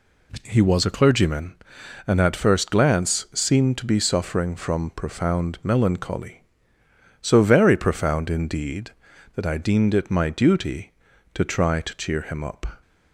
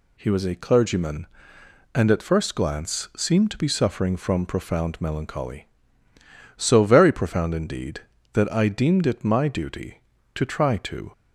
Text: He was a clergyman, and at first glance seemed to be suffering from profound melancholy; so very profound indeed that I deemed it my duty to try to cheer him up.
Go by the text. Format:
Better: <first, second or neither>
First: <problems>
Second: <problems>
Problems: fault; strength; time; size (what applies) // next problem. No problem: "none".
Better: first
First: none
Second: stops before "cheer him up"; at 11.1 s